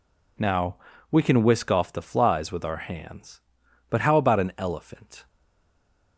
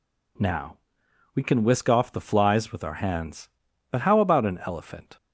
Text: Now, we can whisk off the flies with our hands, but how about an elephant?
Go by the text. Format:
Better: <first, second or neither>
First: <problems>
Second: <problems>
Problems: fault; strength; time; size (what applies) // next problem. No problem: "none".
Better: second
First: stays silent after the last word; slight; from 5.2 s on; 0.9 s long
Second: none